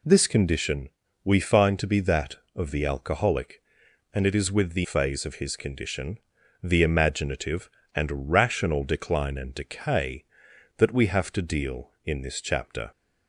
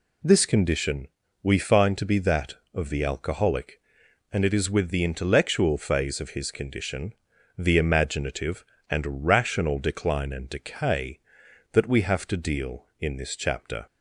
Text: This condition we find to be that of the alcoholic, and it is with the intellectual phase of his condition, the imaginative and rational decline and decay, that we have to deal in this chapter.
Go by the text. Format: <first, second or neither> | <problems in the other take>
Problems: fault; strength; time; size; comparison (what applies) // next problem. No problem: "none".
second | pauses between "condition" and "we"; slight; at 0.8 s; 0.36 s long; slight in the second // skips "intellectual"; at 4.8 s